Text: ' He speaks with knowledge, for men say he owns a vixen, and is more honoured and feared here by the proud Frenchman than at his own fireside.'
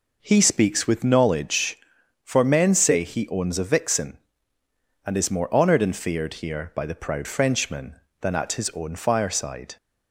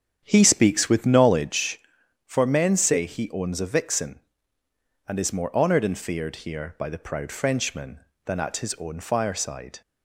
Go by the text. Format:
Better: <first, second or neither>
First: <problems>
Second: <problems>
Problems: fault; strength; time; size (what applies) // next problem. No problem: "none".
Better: first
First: none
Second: starts louder than the rest; strong; until 1.6 s; 8.5 dB